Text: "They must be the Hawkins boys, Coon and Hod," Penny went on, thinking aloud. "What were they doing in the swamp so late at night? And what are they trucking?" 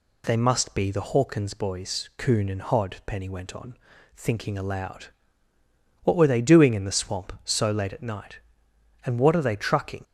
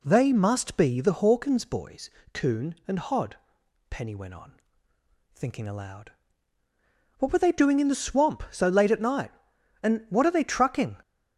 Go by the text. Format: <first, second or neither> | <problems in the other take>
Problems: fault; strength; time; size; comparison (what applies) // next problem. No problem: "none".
neither | none